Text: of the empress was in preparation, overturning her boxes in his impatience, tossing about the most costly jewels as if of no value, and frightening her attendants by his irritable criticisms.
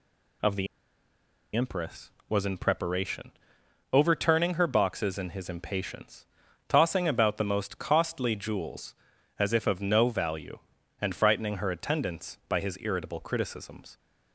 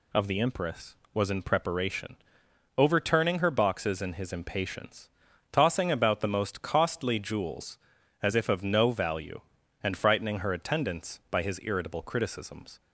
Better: second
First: pauses between "the" and "empress"; noticeable; at 0.6 s; 0.89 s long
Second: none

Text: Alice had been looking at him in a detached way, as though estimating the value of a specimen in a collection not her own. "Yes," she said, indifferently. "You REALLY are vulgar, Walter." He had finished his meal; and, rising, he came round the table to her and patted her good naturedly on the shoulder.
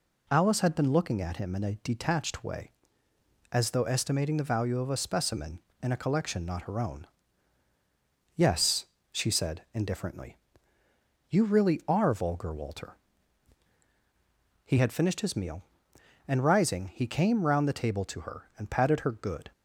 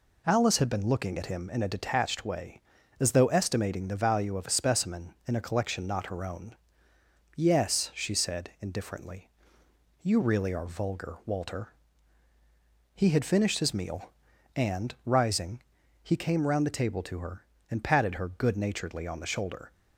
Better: second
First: stops before "naturedly on the shoulder"; at 19.5 s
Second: none

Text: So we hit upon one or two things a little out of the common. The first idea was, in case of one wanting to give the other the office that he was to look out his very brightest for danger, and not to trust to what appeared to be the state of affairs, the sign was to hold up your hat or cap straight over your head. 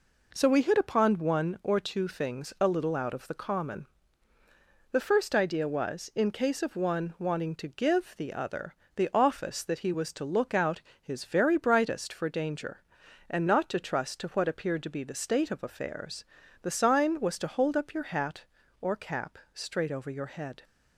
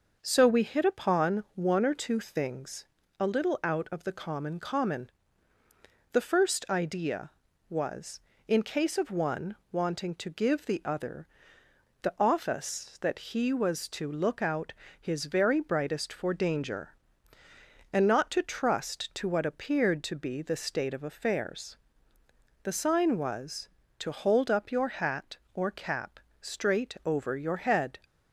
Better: first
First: pauses between "other" and "the"; slight; at 8.7 s; 0.22 s long // pauses between "out" and "his"; slight; at 10.8 s; 0.20 s long // pauses between "cap" and "straight"; slight; at 19.3 s; 0.16 s long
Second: pauses between "things" and "a"; slight; at 2.8 s; 0.34 s long // says "common" twice; at 4.5 s // pauses between "one" and "wanting"; slight; at 9.5 s; 0.16 s long // pauses between "other" and "the"; noticeable; at 11.2 s; 0.74 s long // pauses between "out" and "his"; slight; at 14.7 s; 0.26 s long // pauses between "cap" and "straight"; slight; at 26.1 s; 0.22 s long

